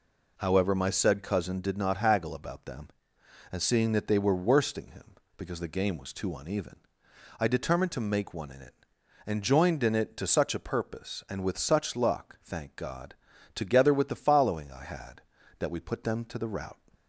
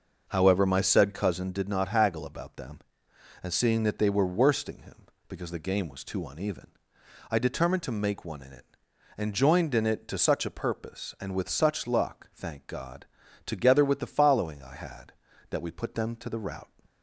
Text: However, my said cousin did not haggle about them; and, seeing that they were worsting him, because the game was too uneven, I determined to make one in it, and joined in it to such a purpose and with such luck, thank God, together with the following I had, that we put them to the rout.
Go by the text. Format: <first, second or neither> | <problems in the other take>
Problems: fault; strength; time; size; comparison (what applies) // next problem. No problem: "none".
first | starts louder than the rest; noticeable; until 1.4 s; 6 dB